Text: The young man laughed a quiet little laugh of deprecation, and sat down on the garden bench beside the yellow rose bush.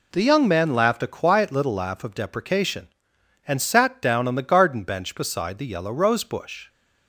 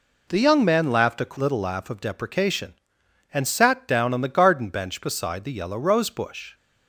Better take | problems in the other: first | skips "quiet"; at 1.3 s

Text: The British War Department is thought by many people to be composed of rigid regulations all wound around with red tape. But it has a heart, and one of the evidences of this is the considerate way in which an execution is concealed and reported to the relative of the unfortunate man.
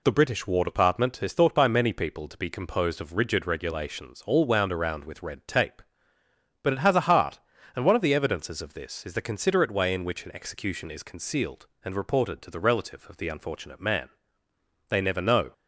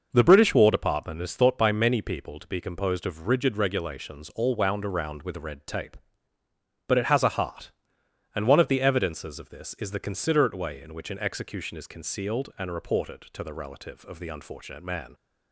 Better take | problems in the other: second | goes on to say "They never know"; noticeable; from 14.8 s on; 0.64 s long

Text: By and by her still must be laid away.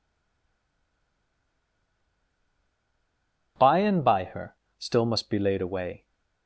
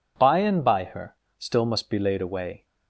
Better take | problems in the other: second | stays silent before the first word; strong; until 3.5 s; 3.5 s long // pauses between "her" and "still"; slight; at 4.5 s; 0.22 s long; slight in the second

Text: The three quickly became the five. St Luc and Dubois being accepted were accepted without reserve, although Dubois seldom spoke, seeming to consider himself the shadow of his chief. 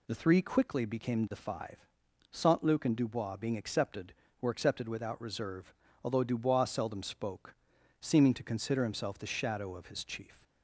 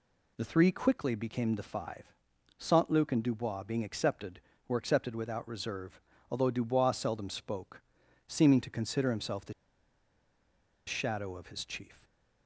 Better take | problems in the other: first | pauses between "the" and "shadow"; strong; at 9.5 s; 1.3 s long

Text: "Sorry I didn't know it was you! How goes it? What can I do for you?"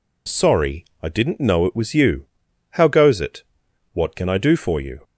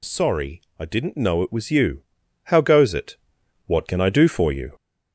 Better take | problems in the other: first | gets louder; noticeable; throughout; 4 dB // pauses between "Sorry" and "I"; slight; at 0.5 s; 0.18 s long; slight in the first

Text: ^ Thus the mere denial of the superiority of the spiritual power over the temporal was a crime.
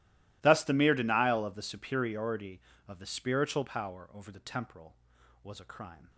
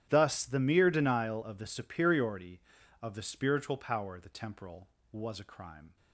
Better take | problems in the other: first | starts louder than the rest; strong; until 1.1 s; 11 dB // skips "over"; at 4.1 s

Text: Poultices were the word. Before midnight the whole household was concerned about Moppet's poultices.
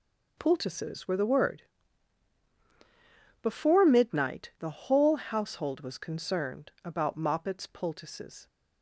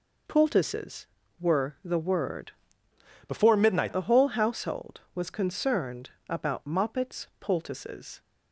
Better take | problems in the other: first | changes voice from "Before" to "midnight"; from 3.2 to 3.9 s; 0.7 s long // pauses between "concerned" and "about"; slight; at 6.0 s; 0.18 s long

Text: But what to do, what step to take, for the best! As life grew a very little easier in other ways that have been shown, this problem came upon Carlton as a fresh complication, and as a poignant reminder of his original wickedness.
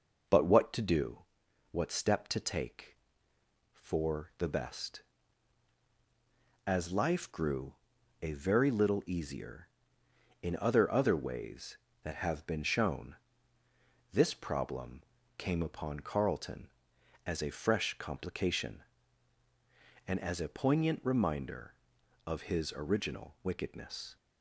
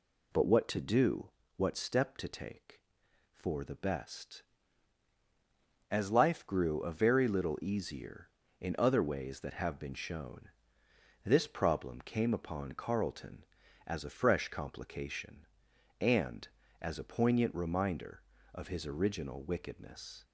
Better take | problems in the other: second | pauses between "grew" and "a"; noticeable; at 7.7 s; 0.46 s long // says "other" twice; at 10.9 s // pauses between "problem" and "came"; slight; at 15.0 s; 0.36 s long

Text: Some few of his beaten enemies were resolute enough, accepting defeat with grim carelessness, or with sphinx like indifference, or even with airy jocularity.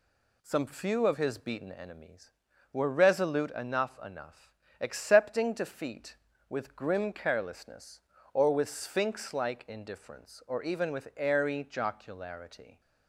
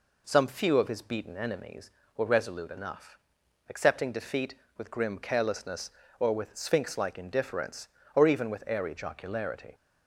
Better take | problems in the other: second | says "enough" twice; at 4.0 s

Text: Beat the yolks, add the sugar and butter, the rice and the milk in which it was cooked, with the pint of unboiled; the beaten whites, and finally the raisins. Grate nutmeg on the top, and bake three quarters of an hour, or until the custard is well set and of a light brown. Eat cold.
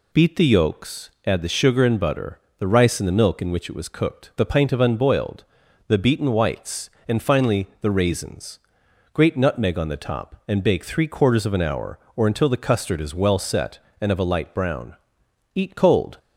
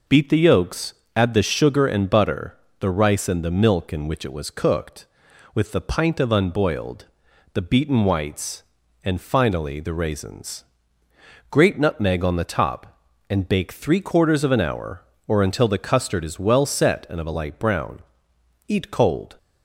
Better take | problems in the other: second | skips "with"; at 4.3 s

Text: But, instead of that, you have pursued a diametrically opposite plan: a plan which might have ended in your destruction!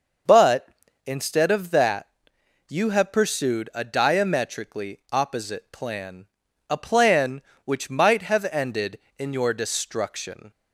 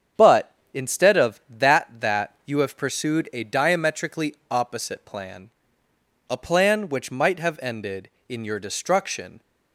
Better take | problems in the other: first | starts louder than the rest; strong; until 1.4 s; 7.5 dB; also in the first // says "that" twice; at 1.9 s

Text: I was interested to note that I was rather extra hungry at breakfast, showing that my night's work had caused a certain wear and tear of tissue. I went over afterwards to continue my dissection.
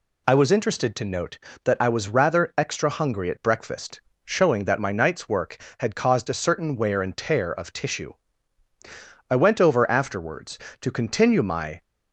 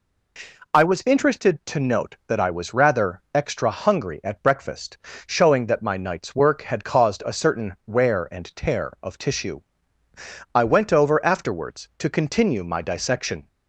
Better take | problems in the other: second | stops before "dissection"; at 11.8 s

